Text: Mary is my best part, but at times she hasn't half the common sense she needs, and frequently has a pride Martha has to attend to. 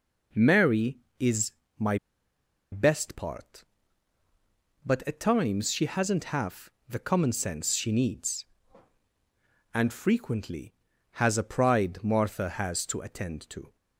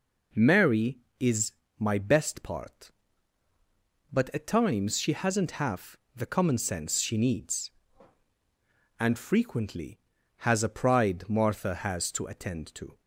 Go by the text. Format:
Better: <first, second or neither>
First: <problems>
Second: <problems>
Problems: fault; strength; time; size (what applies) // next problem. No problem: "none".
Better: second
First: pauses between "is" and "my"; slight; at 1.5 s; 0.26 s long // pauses between "my" and "best"; noticeable; at 1.9 s; 0.74 s long // pauses between "half" and "the"; slight; at 6.7 s; 0.18 s long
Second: pauses between "is" and "my"; slight; at 1.5 s; 0.26 s long // pauses between "half" and "the"; slight; at 5.9 s; 0.18 s long